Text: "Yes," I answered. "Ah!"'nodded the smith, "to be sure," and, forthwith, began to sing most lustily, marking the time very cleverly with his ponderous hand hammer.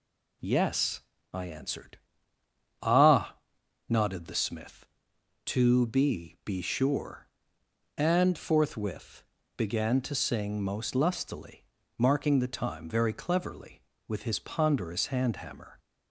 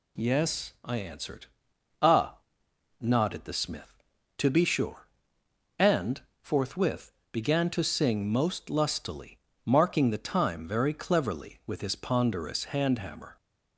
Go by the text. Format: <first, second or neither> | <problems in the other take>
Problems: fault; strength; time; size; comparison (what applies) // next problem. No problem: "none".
second | says "be" twice; at 6.4 s